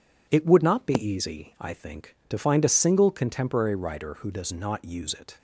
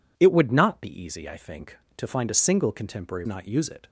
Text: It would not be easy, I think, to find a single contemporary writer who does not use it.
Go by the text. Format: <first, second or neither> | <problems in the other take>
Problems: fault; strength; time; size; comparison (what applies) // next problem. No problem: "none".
first | skips "writer who does"; at 3.2 s